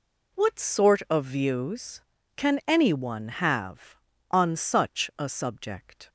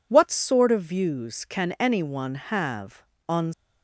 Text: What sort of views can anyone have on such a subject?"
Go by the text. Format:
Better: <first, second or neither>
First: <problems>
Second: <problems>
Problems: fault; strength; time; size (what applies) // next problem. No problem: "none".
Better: first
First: none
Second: stops before "such a subject"; at 3.5 s